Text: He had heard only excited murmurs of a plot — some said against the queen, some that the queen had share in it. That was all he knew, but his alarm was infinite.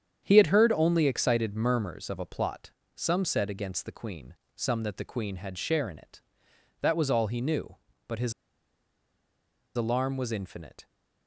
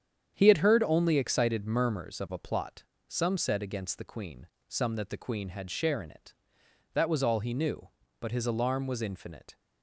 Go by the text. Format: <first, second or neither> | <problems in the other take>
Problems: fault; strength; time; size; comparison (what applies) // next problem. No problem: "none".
second | starts louder than the rest; strong; until 1.2 s; 8.5 dB; strong in the second // pauses between "his" and "alarm"; strong; at 8.3 s; 1.4 s long